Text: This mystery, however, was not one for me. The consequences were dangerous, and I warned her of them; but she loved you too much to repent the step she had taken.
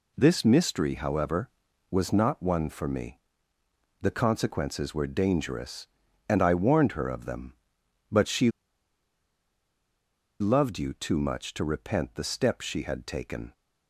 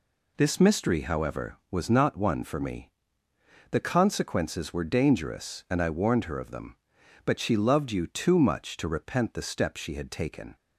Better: second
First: pauses between "she" and "loved"; strong; at 8.5 s; 1.8 s long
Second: none

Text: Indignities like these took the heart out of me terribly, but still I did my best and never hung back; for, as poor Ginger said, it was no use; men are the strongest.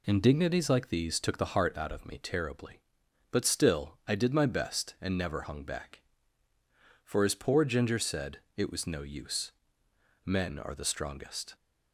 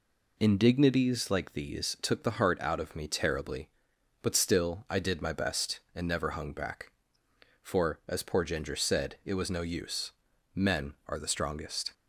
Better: neither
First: none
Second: none

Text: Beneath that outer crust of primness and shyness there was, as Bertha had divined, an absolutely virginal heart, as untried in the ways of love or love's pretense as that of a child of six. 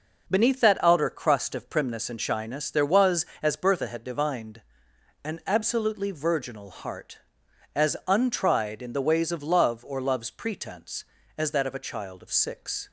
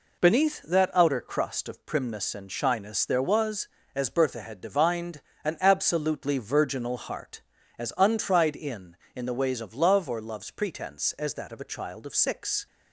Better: first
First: none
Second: says "in" twice; at 9.1 s

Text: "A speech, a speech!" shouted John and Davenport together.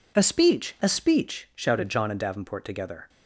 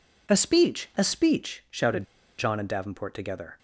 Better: first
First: none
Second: pauses between "shouted" and "John"; slight; at 2.0 s; 0.33 s long

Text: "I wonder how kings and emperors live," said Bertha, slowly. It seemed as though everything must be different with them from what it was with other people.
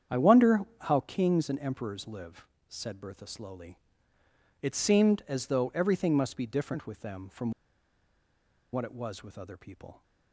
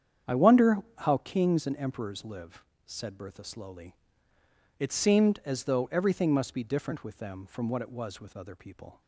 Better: second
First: starts louder than the rest; strong; until 1.3 s; 8.5 dB // pauses between "wonder" and "how"; slight; at 0.6 s; 0.20 s long // pauses between "from" and "what"; at 7.5 s; 1.2 s long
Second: starts louder than the rest; strong; until 1.5 s; 8.5 dB // pauses between "wonder" and "how"; slight; at 0.7 s; 0.20 s long

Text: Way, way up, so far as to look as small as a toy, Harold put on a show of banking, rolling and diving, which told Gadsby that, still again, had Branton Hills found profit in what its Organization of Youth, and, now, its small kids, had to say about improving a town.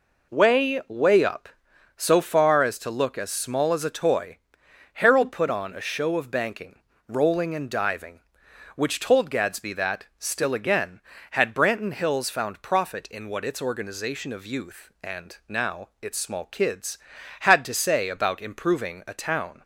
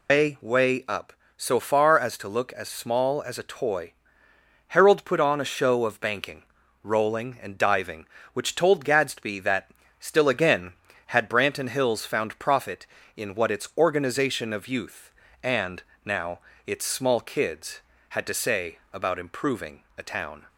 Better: first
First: none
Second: loses the start of "Way"; at 0.0 s; 155 ms // pauses between "improving" and "a"; slight; at 19.8 s; 0.16 s long

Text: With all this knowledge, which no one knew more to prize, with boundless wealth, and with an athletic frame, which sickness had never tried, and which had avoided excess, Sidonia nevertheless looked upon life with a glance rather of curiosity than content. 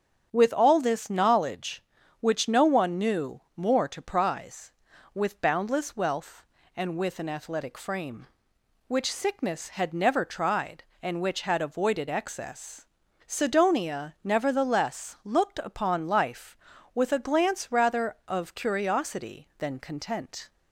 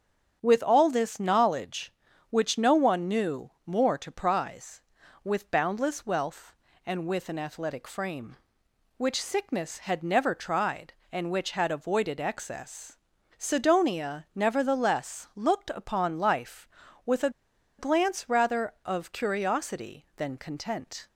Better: first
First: starts louder than the rest; strong; until 1.3 s; 7.5 dB // pauses between "knew" and "more"; slight; at 3.3 s; 0.16 s long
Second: starts louder than the rest; strong; until 1.4 s; 8 dB // pauses between "knew" and "more"; slight; at 3.4 s; 0.16 s long // pauses between "a" and "glance"; noticeable; at 17.2 s; 0.49 s long

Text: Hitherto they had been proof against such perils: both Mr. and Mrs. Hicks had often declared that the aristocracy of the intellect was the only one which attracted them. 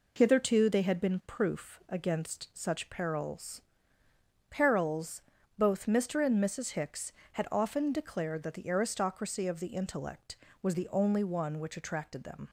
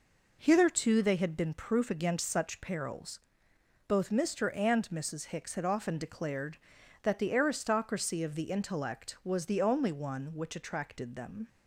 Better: second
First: says "perils" twice; at 4.4 s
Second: none

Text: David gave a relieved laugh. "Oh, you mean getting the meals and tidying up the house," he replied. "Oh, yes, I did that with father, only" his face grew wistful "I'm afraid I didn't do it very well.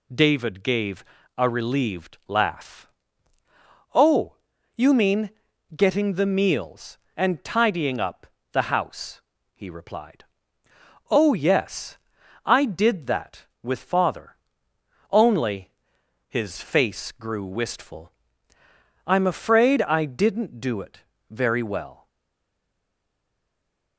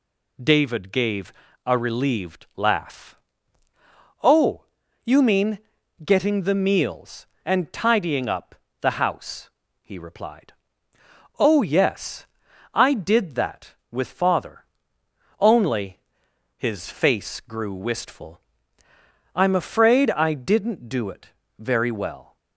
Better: second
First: pauses between "gave" and "a"; slight; at 1.0 s; 0.34 s long // pauses between "mean" and "getting"; at 5.3 s; 0.44 s long // pauses between "up" and "the"; slight; at 8.2 s; 0.26 s long // pauses between "only" and "his"; noticeable; at 15.7 s; 0.58 s long // pauses between "wistful" and "I'm"; noticeable; at 18.1 s; 0.92 s long // pauses between "it" and "very"; slight; at 21.0 s; 0.28 s long // stays silent after the last word; noticeable; from 22.0 s on; 1.9 s long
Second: pauses between "gave" and "a"; slight; at 1.3 s; 0.34 s long // pauses between "mean" and "getting"; at 5.5 s; 0.44 s long // pauses between "up" and "the"; slight; at 8.5 s; 0.26 s long // pauses between "only" and "his"; noticeable; at 15.9 s; 0.58 s long // pauses between "wistful" and "I'm"; noticeable; at 18.4 s; 0.92 s long // pauses between "it" and "very"; slight; at 21.2 s; 0.28 s long

